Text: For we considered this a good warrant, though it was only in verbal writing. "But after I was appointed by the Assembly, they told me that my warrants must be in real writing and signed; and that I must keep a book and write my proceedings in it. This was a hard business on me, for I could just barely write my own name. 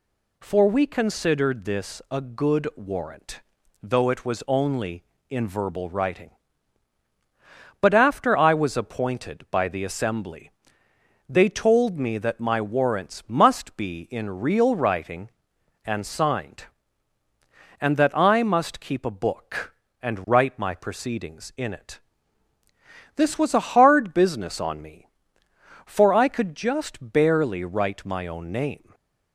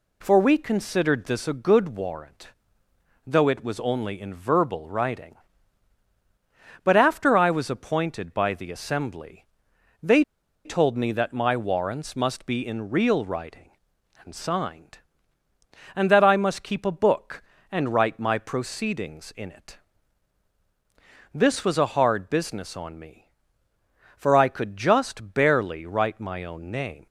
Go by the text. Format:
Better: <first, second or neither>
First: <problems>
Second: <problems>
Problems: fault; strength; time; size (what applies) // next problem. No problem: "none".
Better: first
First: none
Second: pauses between "they" and "told"; at 10.2 s; 0.41 s long